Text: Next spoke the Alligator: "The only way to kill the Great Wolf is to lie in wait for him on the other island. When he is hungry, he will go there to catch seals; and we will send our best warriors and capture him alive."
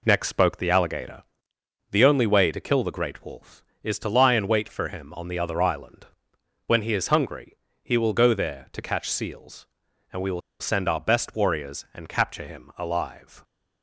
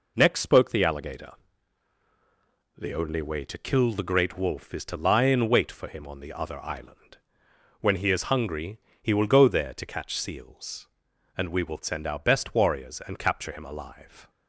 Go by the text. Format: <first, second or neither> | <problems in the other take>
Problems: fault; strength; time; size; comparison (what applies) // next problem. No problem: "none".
second | pauses between "will" and "send"; slight; at 10.4 s; 0.20 s long